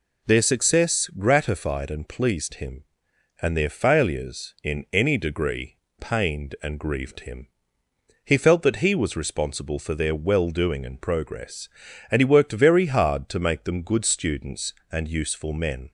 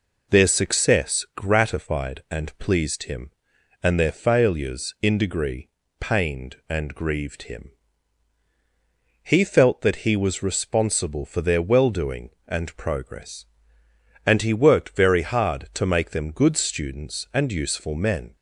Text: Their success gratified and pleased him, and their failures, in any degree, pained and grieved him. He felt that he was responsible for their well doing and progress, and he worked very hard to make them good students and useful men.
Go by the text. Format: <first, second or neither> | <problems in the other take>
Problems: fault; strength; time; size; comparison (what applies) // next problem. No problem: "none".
first | skips "any"; at 5.1 s